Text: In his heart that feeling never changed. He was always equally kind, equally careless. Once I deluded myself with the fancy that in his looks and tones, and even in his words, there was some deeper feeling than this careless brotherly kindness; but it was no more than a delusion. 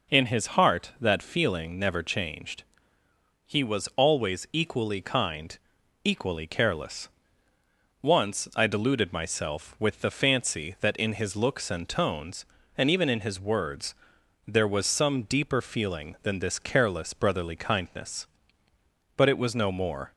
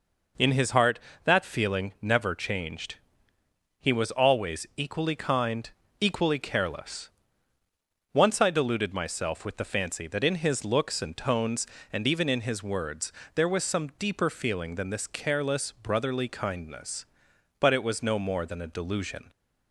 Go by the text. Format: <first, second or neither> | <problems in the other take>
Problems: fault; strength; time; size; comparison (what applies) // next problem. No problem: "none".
second | stops before "than a delusion"; at 20.1 s